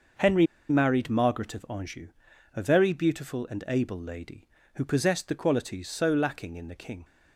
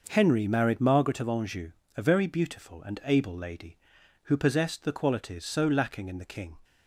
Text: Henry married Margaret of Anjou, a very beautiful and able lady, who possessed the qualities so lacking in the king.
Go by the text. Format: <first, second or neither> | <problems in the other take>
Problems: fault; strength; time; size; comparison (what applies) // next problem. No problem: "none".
second | starts louder than the rest; noticeable; until 1.4 s; 6 dB // pauses between "Henry" and "married"; slight; at 0.4 s; 0.24 s long